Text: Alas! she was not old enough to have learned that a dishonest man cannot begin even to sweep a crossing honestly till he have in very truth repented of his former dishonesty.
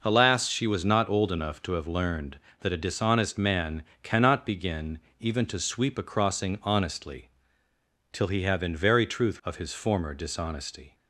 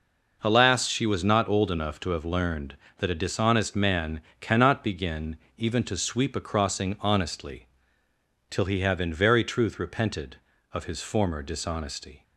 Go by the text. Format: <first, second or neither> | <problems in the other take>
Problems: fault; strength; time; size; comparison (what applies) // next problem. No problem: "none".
second | pauses between "man" and "cannot"; slight; at 3.8 s; 0.18 s long; slight in the second // pauses between "begin" and "even"; slight; at 4.9 s; 0.20 s long; slight in the second // pauses between "honestly" and "till"; noticeable; at 7.2 s; 0.82 s long; noticeable in the second // skips "repented"; at 9.4 s